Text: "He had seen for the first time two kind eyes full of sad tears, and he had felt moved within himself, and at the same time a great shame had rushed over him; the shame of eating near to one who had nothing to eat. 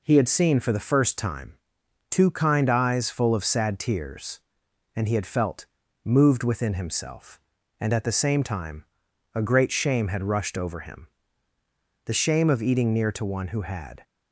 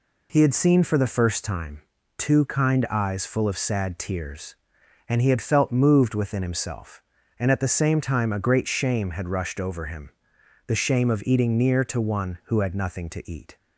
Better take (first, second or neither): second